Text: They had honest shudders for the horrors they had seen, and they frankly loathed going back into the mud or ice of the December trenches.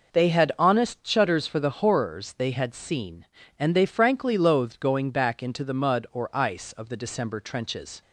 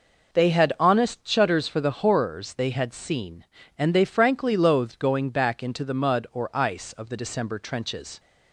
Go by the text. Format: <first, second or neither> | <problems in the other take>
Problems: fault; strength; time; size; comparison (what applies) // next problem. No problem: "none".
neither | none